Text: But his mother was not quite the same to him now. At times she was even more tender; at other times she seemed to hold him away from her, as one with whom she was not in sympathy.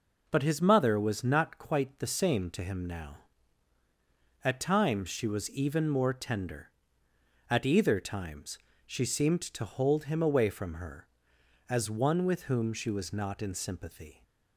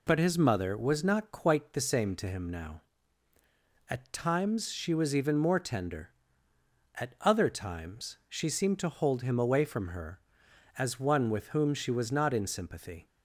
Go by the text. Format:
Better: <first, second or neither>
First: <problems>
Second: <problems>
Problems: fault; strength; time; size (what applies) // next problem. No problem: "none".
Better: second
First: says "either" for "other"; at 7.6 s // pauses between "times" and "she"; slight; at 8.5 s; 0.26 s long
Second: none